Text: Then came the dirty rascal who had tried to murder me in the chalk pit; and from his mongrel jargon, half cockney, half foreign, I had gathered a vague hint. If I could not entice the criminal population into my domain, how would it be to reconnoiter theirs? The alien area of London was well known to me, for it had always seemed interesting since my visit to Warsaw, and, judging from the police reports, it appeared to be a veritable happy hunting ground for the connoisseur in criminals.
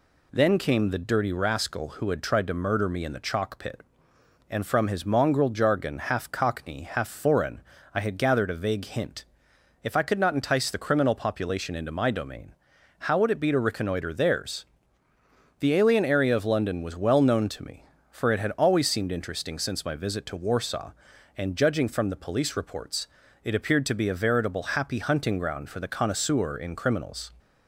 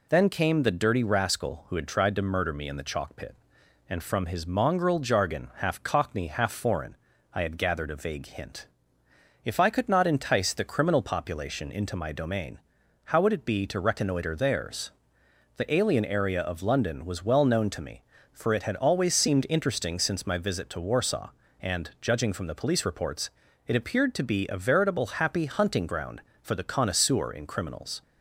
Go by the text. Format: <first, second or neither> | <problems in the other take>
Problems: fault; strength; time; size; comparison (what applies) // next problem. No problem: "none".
neither | none